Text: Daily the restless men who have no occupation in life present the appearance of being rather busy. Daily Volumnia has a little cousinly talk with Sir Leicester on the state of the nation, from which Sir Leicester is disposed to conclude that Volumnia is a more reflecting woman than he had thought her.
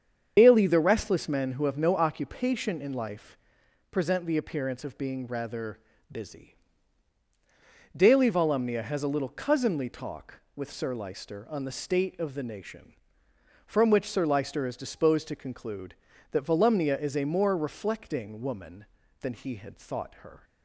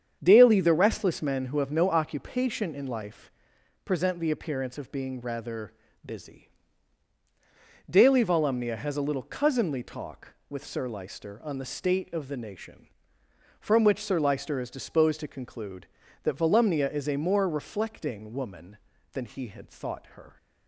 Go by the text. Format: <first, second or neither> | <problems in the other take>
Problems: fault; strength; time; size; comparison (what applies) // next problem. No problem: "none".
second | loses the start of "Daily"; at 0.3 s; 100 ms // starts louder than the rest; strong; until 1.3 s; 7.5 dB; strong in the second // pauses between "life" and "present"; noticeable; at 3.3 s; 0.54 s long; noticeable in the second // pauses between "rather" and "busy"; slight; at 5.7 s; 0.34 s long; slight in the second